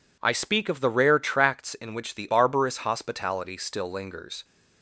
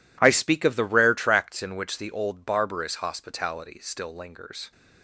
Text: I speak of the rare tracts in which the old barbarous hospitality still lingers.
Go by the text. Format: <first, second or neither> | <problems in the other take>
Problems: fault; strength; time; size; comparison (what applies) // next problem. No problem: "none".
second | skips "old"; at 2.2 s